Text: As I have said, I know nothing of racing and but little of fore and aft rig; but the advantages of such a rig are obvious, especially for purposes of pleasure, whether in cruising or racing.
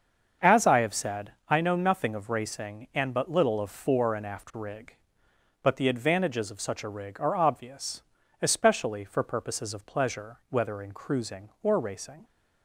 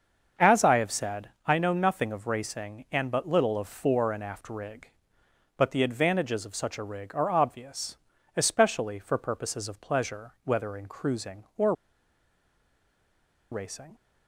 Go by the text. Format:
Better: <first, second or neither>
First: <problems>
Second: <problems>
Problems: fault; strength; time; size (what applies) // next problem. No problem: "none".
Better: first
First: starts louder than the rest; until 1.6 s; 7 dB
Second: starts louder than the rest; until 1.5 s; 6.5 dB // pauses between "or" and "racing"; strong; at 11.7 s; 1.7 s long